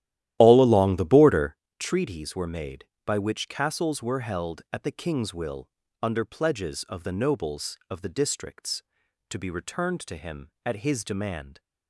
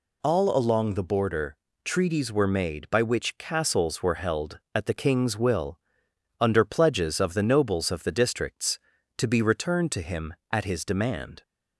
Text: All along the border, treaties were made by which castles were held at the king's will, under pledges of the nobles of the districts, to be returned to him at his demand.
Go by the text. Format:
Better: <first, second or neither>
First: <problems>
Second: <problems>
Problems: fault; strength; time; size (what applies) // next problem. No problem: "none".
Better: second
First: starts louder than the rest; strong; until 1.7 s; 13 dB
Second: none